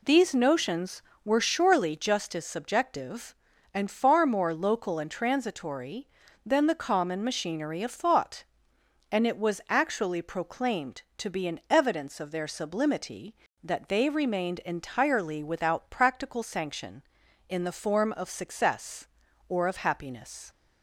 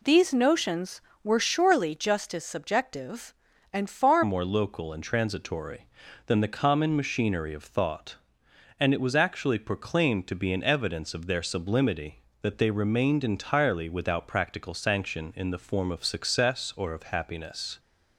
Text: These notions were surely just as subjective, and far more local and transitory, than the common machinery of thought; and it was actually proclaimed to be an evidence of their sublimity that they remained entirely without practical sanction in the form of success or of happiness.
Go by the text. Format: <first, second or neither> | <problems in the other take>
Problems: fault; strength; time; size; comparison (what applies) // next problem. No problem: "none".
first | changes voice at "more"; from 4.2 s on; 13.5 s long